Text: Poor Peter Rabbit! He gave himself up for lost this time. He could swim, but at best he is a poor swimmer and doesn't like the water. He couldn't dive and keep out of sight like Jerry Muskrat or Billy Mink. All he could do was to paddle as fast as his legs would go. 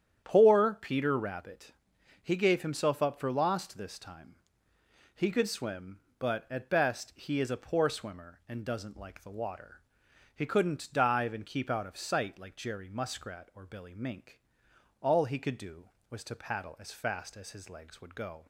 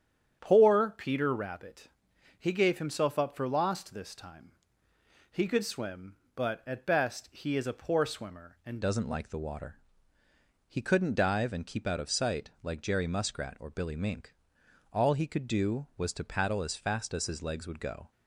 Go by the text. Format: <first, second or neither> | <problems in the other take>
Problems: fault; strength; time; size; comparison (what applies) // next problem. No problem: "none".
first | starts louder than the rest; strong; until 1.4 s; 8.5 dB; strong in the first // changes voice at "doesn't"; from 8.8 s on; 9.3 s long